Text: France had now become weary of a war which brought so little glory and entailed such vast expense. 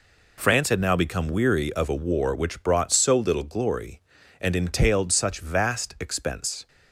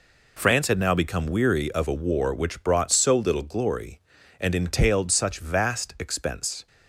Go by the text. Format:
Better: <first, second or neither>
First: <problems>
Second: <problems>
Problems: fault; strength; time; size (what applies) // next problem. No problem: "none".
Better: neither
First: none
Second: none